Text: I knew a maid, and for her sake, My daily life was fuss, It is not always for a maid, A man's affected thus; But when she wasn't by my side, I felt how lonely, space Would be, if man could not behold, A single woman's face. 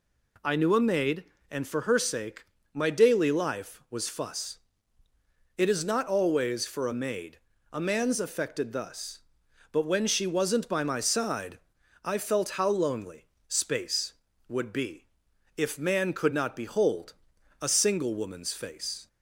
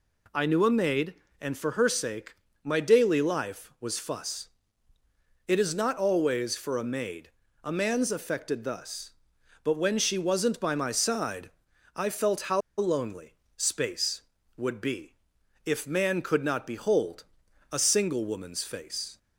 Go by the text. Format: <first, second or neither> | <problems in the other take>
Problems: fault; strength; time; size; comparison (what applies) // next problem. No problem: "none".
first | pauses between "how" and "lonely"; slight; at 12.6 s; 0.17 s long